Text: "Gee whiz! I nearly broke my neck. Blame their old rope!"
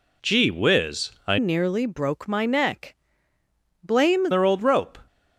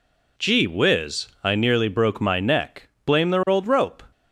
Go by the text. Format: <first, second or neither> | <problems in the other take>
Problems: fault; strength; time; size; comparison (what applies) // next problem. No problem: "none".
second | changes voice from "nearly" to "Blame"; from 1.3 to 4.2 s; 2.9 s long